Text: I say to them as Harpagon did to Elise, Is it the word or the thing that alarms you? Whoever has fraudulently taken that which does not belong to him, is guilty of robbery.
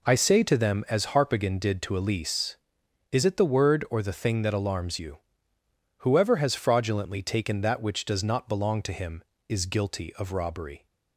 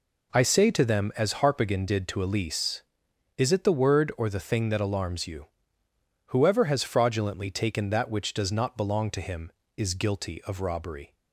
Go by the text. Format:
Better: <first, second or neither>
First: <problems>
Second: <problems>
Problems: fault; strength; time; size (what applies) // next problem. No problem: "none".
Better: neither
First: none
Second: none